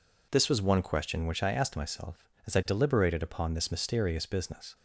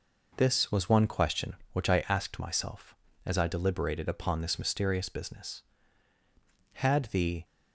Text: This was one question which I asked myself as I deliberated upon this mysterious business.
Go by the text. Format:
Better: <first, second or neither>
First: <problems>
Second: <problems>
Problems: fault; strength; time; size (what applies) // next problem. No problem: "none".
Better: first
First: none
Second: goes on to say "Had the"; noticeable; from 6.7 s on; 0.70 s long